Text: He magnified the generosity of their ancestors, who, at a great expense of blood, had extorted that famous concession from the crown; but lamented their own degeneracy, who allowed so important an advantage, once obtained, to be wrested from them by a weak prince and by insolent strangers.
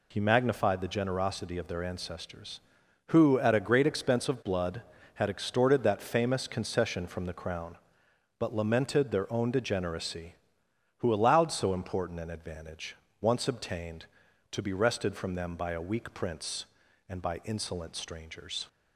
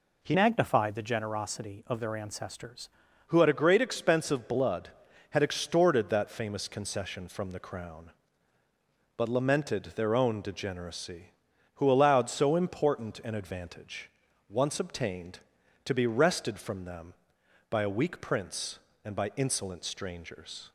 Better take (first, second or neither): first